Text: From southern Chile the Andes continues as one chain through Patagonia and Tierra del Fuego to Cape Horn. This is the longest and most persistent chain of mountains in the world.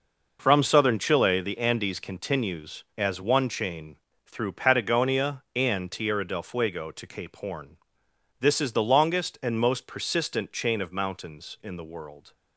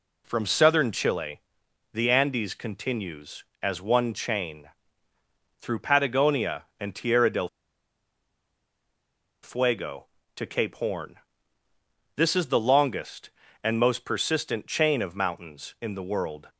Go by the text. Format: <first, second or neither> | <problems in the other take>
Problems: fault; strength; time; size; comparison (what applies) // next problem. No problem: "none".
first | pauses between "Chile" and "the"; noticeable; at 1.3 s; 0.54 s long // pauses between "chain" and "through"; noticeable; at 4.6 s; 0.94 s long; slight in the first // pauses between "del" and "Fuego"; strong; at 7.4 s; 1.9 s long